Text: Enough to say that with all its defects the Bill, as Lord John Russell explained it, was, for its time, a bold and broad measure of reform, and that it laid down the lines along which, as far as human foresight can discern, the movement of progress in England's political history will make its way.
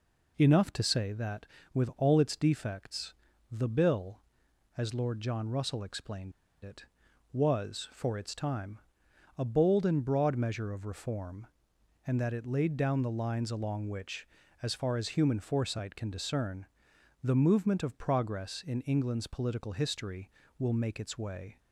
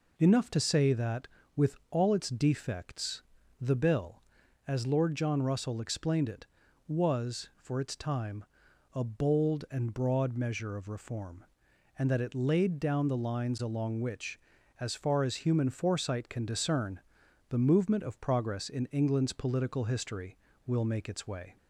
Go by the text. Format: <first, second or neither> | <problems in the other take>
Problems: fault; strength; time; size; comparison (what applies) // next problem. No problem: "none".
second | pauses between "defects" and "the"; at 3.1 s; 0.38 s long; also in the second // pauses between "explained" and "it"; slight; at 6.3 s; 0.32 s long